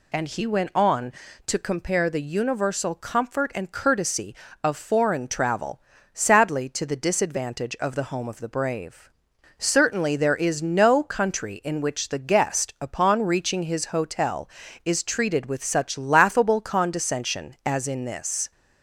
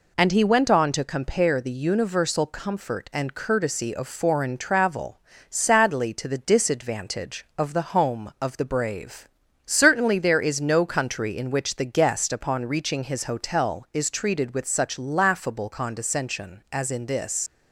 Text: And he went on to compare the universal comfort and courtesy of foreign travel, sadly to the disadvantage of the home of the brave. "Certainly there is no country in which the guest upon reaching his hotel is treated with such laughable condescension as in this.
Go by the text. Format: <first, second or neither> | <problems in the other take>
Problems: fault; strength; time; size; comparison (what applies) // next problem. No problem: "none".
first | leaves "this" unfinished; at 17.4 s; 75 ms